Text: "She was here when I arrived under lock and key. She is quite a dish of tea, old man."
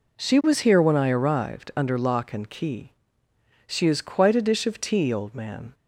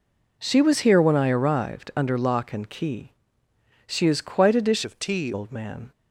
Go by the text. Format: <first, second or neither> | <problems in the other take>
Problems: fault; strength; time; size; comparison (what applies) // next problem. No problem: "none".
first | changes voice from "of" to "tea"; from 4.8 to 5.3 s; 0.5 s long